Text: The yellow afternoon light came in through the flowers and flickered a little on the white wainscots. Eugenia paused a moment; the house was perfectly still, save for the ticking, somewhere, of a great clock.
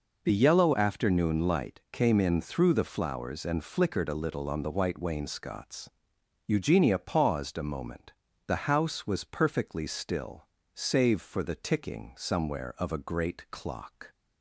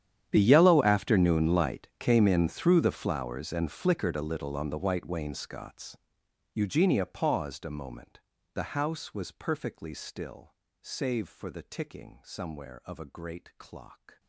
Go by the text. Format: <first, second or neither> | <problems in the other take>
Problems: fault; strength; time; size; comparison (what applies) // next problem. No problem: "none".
first | gets quieter; strong; throughout; 23 dB